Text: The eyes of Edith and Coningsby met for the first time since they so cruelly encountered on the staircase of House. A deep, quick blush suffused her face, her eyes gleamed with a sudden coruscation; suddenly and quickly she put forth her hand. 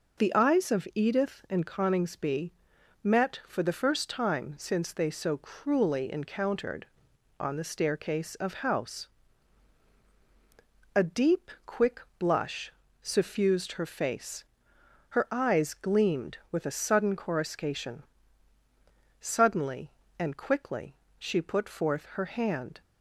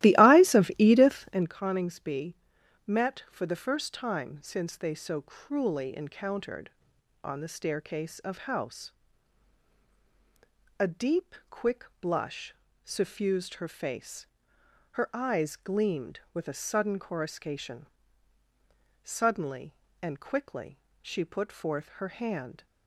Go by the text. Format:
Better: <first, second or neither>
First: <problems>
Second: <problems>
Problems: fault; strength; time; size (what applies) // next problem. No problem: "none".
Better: first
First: pauses between "Coningsby" and "met"; noticeable; at 2.5 s; 0.54 s long // pauses between "quick" and "blush"; slight; at 11.9 s; 0.18 s long // pauses between "blush" and "suffused"; slight; at 12.7 s; 0.28 s long // pauses between "quickly" and "she"; slight; at 20.9 s; 0.24 s long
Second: starts louder than the rest; strong; until 1.5 s; 15.5 dB // pauses between "Coningsby" and "met"; noticeable; at 2.3 s; 0.54 s long // pauses between "quick" and "blush"; slight; at 11.8 s; 0.18 s long // pauses between "blush" and "suffused"; slight; at 12.5 s; 0.28 s long // pauses between "quickly" and "she"; slight; at 20.7 s; 0.24 s long